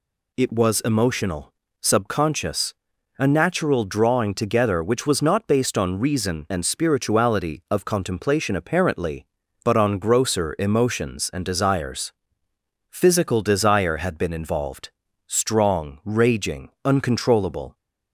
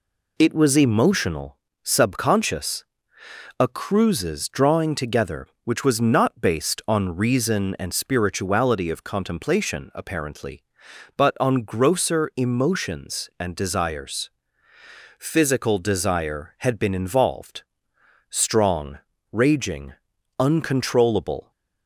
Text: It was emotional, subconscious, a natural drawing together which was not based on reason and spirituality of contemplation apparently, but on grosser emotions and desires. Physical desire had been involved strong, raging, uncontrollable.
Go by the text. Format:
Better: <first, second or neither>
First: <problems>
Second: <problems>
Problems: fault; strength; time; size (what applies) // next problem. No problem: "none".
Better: first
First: pauses between "involved" and "strong"; at 14.8 s; 0.38 s long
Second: says "cruises" for "natural"; at 3.6 s // pauses between "involved" and "strong"; noticeable; at 17.6 s; 0.66 s long